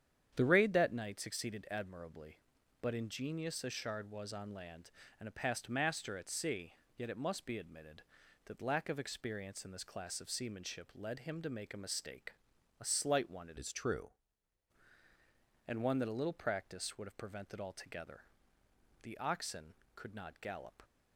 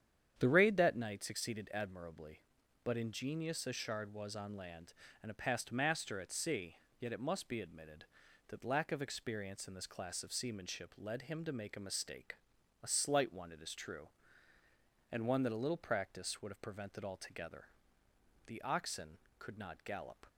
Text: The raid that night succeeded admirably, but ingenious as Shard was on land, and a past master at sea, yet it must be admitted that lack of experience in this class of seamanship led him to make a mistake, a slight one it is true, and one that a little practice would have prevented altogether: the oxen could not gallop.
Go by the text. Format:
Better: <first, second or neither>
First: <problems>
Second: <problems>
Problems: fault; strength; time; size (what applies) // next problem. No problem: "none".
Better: second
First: starts louder than the rest; strong; until 1.3 s; 9 dB // changes voice from "is" to "true"; from 13.5 to 14.1 s; 0.6 s long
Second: starts louder than the rest; strong; until 1.3 s; 9 dB